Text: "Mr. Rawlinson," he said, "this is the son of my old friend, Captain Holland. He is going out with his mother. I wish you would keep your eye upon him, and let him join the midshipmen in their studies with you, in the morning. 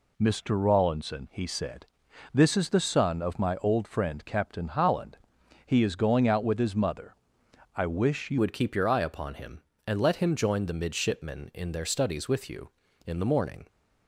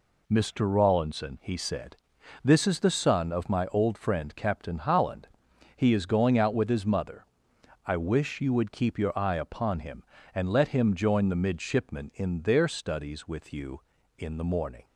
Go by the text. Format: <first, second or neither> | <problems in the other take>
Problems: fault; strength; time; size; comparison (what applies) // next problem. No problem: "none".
second | changes voice at "would"; from 8.3 s on; 5.3 s long